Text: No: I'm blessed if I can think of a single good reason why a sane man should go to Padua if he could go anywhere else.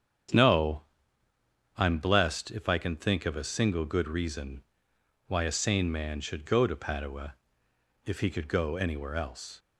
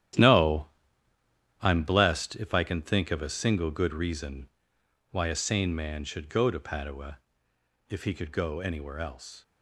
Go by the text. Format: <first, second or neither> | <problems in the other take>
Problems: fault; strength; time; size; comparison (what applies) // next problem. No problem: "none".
first | gets quieter; strong; throughout; 10 dB // starts louder than the rest; strong; until 2.0 s; 11.5 dB; strong in the first // pauses between "reason" and "why"; noticeable; at 4.4 s; 0.62 s long; noticeable in the first // pauses between "Padua" and "if"; noticeable; at 7.1 s; 0.70 s long; noticeable in the first